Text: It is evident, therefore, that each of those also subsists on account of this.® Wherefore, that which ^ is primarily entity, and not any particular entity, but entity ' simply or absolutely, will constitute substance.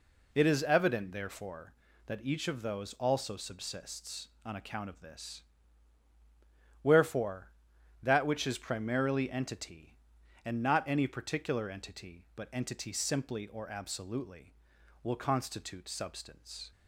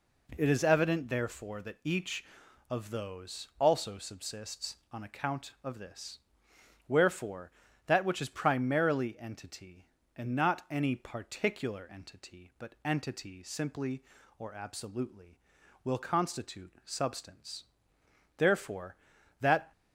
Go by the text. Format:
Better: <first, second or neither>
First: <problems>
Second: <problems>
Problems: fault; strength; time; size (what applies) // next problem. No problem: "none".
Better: first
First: none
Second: goes on to say "Therefore that"; from 18.3 s on; 1.3 s long